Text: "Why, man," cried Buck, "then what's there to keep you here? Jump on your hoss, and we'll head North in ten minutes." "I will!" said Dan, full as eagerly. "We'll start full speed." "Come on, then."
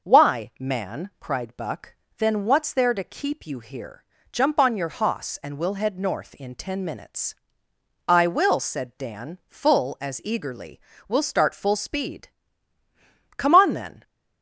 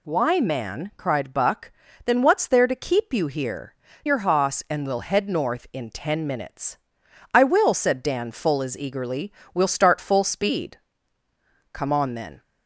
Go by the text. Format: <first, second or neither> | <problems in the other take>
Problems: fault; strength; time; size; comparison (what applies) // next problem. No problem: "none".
first | skips "Jump on"; at 3.8 s